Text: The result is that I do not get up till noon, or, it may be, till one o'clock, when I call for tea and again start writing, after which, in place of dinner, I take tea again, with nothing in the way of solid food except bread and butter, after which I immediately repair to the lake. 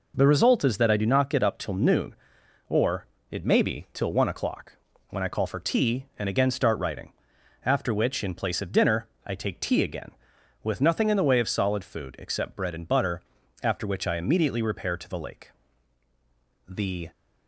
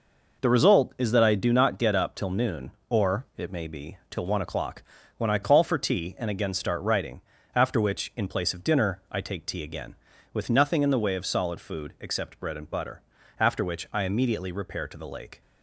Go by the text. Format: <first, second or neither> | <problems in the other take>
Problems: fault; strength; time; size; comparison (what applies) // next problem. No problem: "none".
second | goes on to say "The"; slight; from 16.6 s on; 0.42 s long